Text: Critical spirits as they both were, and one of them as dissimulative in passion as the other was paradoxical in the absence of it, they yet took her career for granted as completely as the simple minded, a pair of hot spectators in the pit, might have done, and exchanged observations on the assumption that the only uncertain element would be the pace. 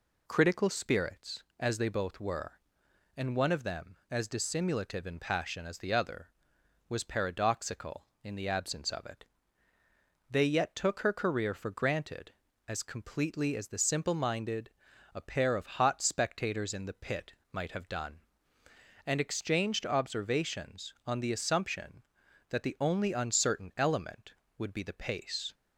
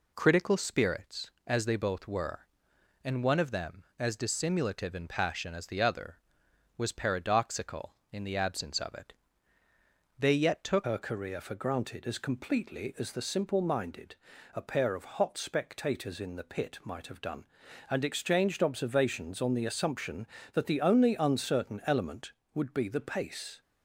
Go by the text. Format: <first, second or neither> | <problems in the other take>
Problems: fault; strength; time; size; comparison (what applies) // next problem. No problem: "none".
first | changes voice at "her"; from 10.8 s on; 12.8 s long